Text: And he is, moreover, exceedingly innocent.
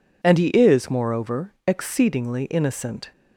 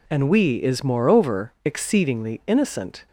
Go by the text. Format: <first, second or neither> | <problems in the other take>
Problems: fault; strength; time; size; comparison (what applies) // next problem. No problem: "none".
first | says "we" for "he"; at 0.2 s